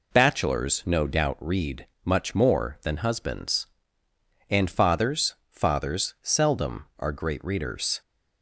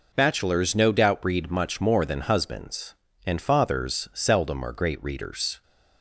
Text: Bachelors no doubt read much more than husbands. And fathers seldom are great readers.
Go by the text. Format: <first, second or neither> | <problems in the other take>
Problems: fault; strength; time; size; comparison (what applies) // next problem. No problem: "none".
second | pauses between "read" and "much"; slight; at 1.8 s; 0.16 s long // says "fathers" twice; at 5.4 s